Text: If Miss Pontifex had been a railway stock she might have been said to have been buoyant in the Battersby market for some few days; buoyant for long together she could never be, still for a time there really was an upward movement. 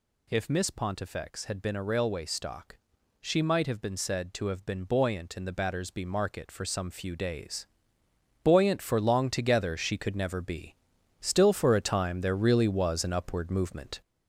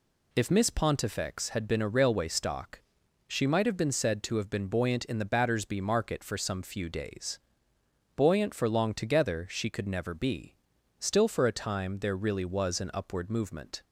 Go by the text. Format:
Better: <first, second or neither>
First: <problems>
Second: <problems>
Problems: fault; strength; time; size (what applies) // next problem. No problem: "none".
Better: second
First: gets louder; noticeable; throughout; 5 dB // pauses between "stock" and "she"; at 2.7 s; 0.44 s long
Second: pauses between "stock" and "she"; noticeable; at 2.7 s; 0.48 s long